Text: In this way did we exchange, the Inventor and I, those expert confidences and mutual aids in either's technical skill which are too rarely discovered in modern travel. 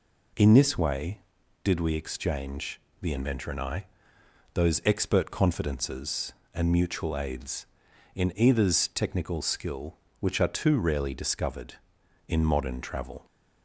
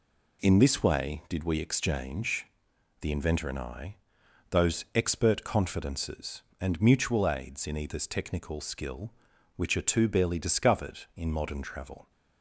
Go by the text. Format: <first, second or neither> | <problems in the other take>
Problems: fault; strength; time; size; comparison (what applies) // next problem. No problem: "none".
first | says "barely" for "rarely"; at 10.0 s